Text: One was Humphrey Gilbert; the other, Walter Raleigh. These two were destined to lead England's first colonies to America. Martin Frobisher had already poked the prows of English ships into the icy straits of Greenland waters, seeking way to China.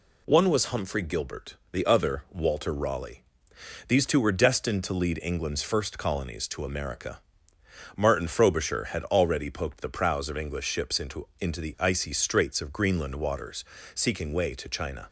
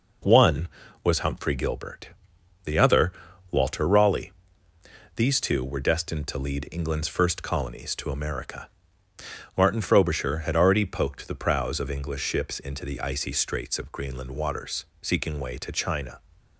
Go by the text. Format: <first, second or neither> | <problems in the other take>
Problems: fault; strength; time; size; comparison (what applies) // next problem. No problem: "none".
second | says "into" twice; at 11.4 s